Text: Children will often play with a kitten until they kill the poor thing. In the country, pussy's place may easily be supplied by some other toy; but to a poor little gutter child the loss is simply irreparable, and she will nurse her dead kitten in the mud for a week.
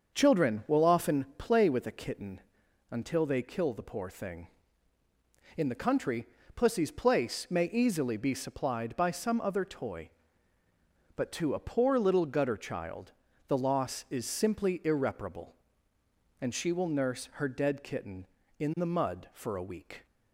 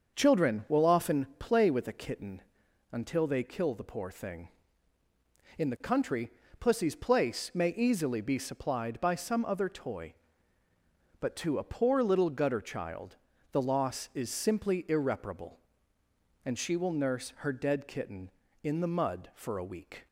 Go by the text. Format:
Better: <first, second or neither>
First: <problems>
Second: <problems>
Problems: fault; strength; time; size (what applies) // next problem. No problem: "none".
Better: neither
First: starts louder than the rest; until 1.1 s; 6.5 dB // pauses between "kitten" and "until"; noticeable; at 2.4 s; 0.50 s long // pauses between "child" and "the"; slight; at 13.1 s; 0.36 s long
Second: starts louder than the rest; until 1.2 s; 6.5 dB // pauses between "kitten" and "until"; noticeable; at 2.4 s; 0.50 s long // pauses between "child" and "the"; slight; at 13.1 s; 0.36 s long